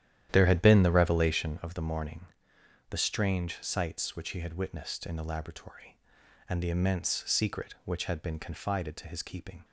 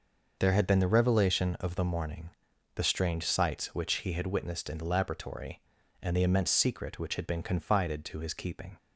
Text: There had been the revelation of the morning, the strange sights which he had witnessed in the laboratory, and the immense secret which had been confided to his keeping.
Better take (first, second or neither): second